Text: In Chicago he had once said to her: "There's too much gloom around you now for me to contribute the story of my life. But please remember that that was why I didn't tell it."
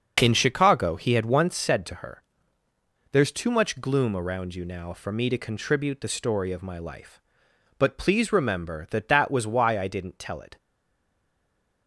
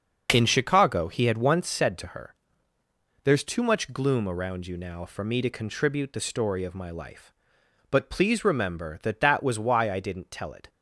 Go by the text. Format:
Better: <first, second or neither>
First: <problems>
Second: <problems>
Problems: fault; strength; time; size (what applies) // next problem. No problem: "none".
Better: second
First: starts louder than the rest; noticeable; until 1.2 s; 6 dB // stays silent after the last word; noticeable; from 10.5 s on; 1.3 s long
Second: starts louder than the rest; noticeable; until 1.3 s; 6 dB